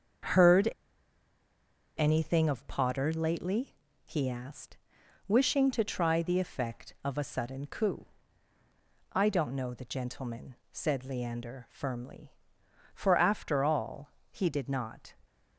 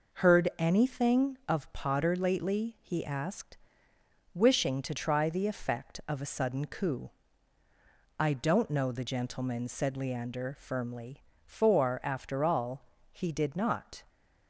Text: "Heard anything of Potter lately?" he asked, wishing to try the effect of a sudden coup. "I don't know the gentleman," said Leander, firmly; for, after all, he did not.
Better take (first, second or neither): second